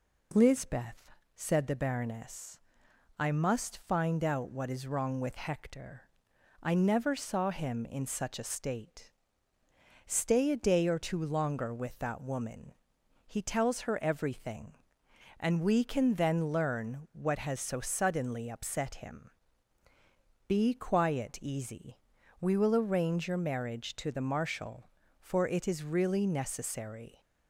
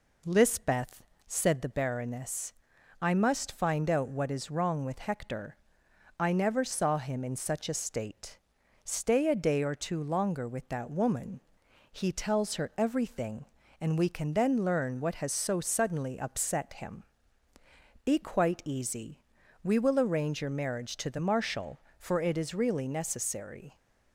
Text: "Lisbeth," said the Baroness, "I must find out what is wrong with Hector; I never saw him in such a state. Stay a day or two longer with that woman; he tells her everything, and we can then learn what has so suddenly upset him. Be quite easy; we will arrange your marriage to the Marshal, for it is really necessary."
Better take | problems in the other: second | says "quiet" for "quite"; at 20.7 s

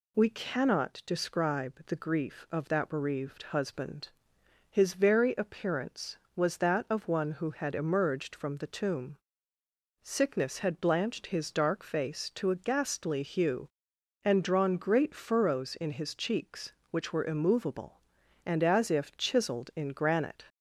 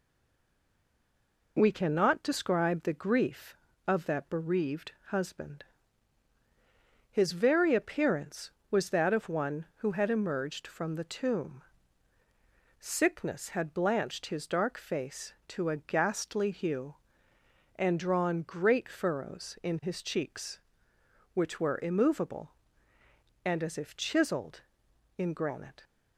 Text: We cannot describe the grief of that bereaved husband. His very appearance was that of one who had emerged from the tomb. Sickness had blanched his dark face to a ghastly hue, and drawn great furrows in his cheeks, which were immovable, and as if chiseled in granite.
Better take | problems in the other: first | stays silent before the first word; noticeable; until 1.5 s; 1.5 s long // pauses between "bereaved" and "husband"; slight; at 4.9 s; 0.16 s long

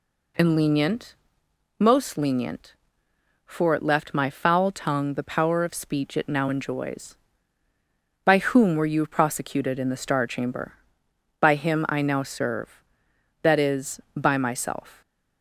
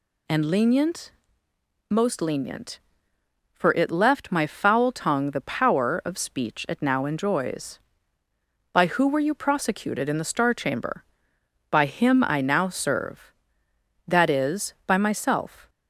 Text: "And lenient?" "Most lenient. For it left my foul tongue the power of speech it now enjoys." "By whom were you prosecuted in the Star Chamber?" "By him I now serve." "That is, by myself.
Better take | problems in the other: first | says "who" for "whom"; at 8.8 s

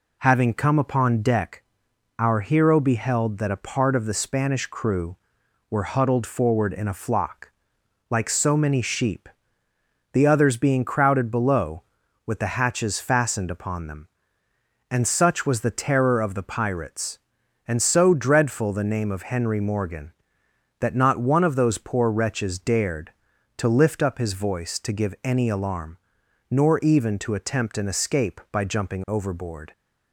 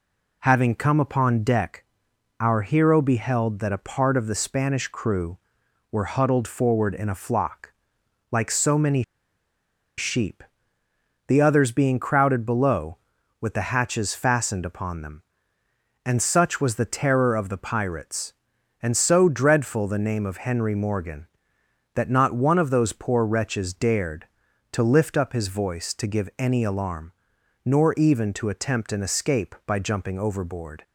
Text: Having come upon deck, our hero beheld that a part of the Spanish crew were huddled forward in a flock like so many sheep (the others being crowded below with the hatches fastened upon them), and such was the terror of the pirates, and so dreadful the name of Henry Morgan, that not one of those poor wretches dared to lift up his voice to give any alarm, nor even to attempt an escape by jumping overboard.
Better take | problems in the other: first | pauses between "flock" and "like"; noticeable; at 7.7 s; 0.58 s long; noticeable in the first // pauses between "many" and "sheep"; noticeable; at 9.0 s; 0.96 s long

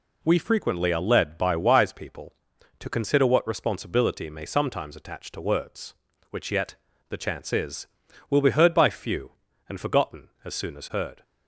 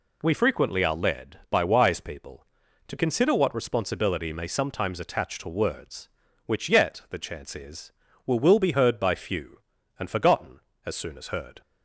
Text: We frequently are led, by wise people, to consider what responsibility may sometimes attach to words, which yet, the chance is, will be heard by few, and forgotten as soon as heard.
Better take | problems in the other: first | says "will" twice; at 8.4 s

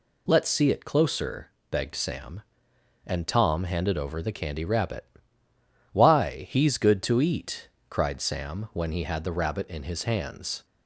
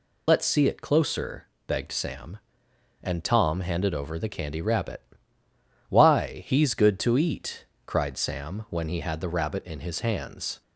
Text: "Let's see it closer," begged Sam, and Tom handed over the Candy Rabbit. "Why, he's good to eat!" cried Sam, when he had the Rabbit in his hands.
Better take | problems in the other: first | loses the start of "Let's"; at 0.2 s; 55 ms

